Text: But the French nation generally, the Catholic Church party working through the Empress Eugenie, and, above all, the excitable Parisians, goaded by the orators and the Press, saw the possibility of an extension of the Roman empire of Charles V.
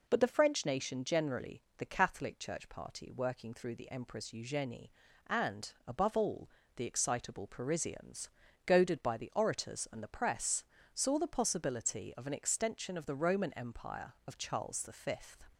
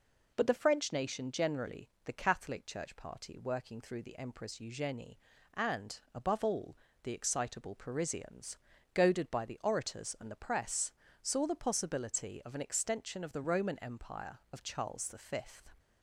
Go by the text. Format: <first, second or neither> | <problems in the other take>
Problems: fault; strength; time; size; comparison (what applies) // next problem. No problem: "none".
neither | none